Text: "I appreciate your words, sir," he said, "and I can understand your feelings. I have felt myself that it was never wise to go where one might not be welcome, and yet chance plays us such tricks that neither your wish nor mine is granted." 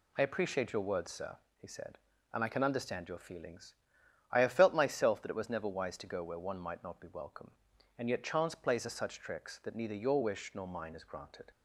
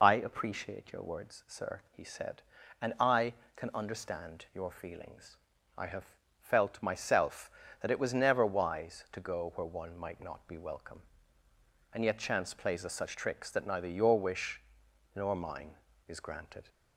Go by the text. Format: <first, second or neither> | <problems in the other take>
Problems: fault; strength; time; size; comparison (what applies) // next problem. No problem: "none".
first | loses the start of "I"; at 0.0 s; 35 ms // pauses between "have" and "felt"; slight; at 6.0 s; 0.34 s long // pauses between "wish" and "nor"; noticeable; at 14.6 s; 0.54 s long